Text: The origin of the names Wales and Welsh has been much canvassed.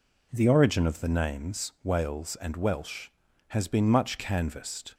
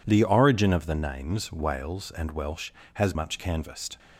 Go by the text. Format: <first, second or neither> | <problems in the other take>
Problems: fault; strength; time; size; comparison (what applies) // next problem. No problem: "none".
first | skips "been"; at 3.1 s